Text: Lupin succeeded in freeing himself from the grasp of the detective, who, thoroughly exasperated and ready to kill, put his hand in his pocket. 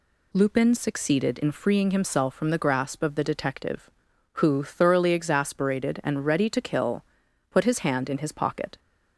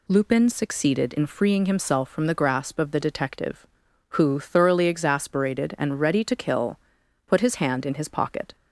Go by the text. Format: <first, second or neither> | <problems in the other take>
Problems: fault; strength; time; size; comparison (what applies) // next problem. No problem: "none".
neither | none